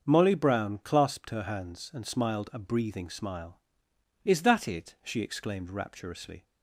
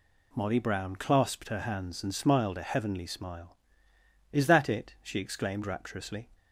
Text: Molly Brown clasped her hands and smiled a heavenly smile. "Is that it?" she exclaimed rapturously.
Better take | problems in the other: second | starts louder than the rest; until 1.0 s; 6.5 dB // says "breathing" for "heavenly"; at 2.5 s

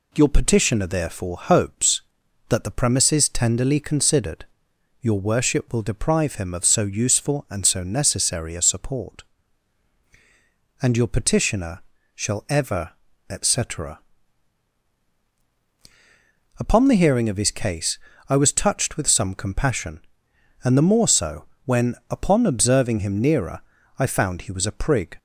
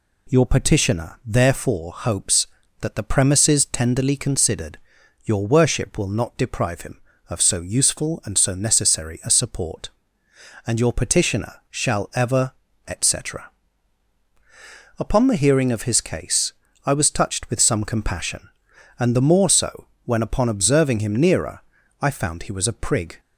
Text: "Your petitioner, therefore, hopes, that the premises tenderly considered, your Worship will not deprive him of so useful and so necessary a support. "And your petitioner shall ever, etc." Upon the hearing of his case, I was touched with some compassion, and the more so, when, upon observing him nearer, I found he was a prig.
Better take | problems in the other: second | skips "not"; at 5.8 s // pauses between "petitioner" and "shall"; slight; at 11.7 s; 0.34 s long

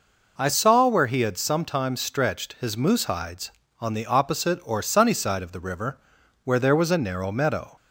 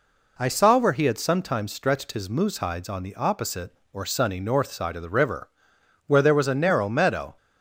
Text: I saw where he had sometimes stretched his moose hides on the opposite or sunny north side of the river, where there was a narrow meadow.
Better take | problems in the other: second | skips "north"; at 5.1 s

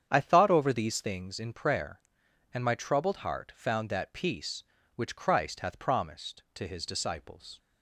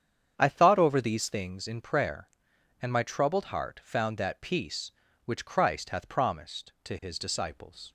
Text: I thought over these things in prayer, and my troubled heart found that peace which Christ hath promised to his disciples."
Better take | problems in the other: neither | starts louder than the rest; strong; the same in both

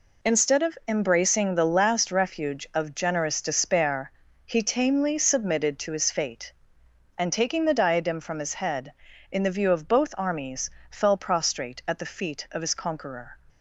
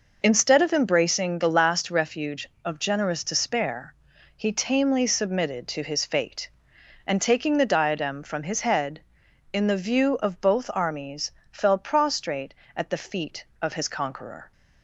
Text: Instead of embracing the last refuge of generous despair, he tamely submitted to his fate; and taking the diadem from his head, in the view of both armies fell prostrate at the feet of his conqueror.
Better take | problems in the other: neither | pauses between "armies" and "fell"; slight; the same in both

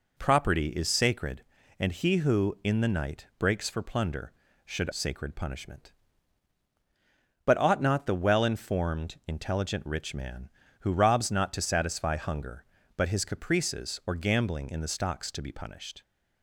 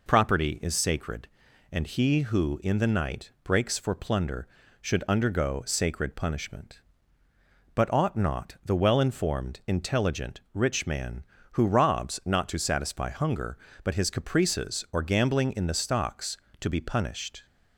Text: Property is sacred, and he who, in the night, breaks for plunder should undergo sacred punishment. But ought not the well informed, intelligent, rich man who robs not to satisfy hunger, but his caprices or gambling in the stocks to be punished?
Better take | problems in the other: second | skips "undergo"; at 4.9 s

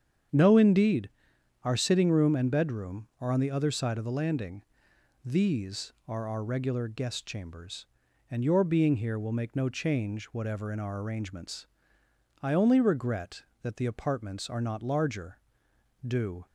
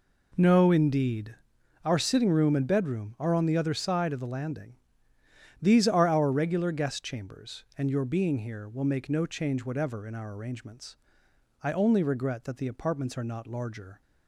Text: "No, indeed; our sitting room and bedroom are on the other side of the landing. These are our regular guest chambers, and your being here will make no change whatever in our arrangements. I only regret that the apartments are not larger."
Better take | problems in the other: second | starts louder than the rest; strong; until 1.8 s; 8 dB // goes on to say "Do"; slight; from 16.0 s on; 0.40 s long

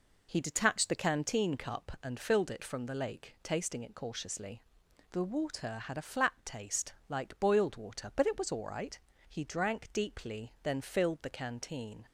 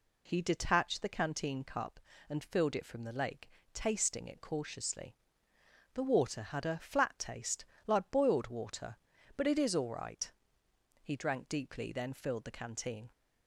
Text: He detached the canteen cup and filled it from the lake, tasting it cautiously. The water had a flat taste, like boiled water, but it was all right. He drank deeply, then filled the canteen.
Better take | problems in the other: first | says "is" for "was"; at 9.5 s

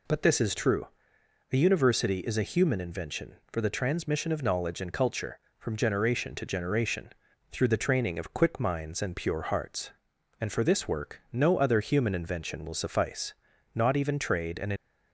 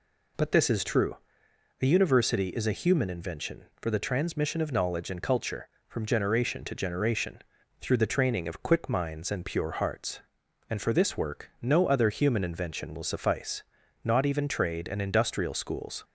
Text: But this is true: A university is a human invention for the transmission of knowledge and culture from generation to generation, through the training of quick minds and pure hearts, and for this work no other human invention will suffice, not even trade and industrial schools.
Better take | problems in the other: second | stops before "industrial schools"; at 14.7 s

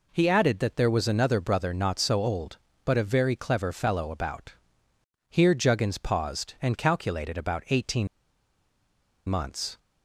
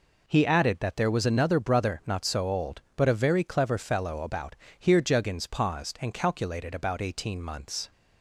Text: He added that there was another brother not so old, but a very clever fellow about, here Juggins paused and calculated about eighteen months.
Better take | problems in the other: second | pauses between "eighteen" and "months"; at 8.0 s; 1.2 s long

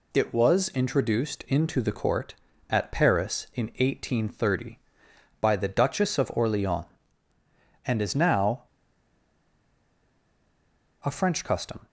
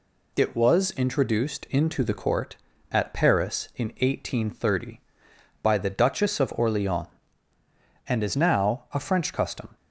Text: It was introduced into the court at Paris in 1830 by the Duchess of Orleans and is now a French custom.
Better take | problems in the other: second | pauses between "now" and "a"; strong; at 8.6 s; 2.4 s long

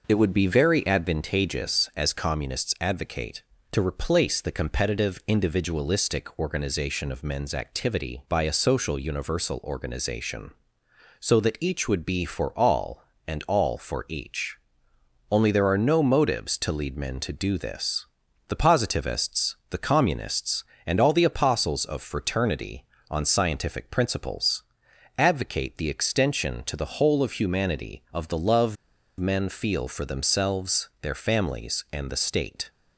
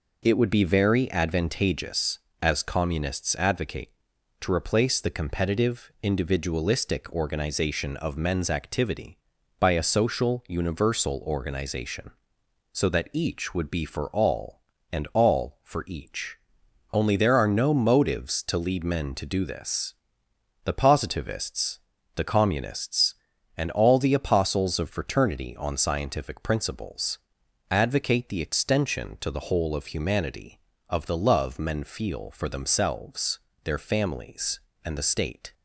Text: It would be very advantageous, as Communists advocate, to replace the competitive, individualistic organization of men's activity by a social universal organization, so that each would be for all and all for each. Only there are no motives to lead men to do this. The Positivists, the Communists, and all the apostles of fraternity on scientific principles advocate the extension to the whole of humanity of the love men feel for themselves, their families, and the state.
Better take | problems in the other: second | pauses between "principles" and "advocate"; noticeable; at 24.6 s; 0.56 s long; noticeable in the second // pauses between "love" and "men"; at 28.7 s; 0.43 s long

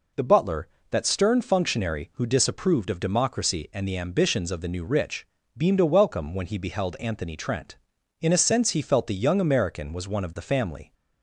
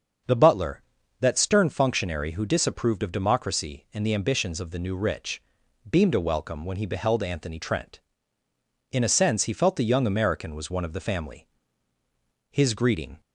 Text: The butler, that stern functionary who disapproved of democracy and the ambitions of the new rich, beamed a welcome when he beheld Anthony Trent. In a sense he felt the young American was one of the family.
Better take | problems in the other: first | starts louder than the rest; until 1.6 s; 7 dB // goes on to say "His greeting"; noticeable; from 12.5 s on; 0.68 s long

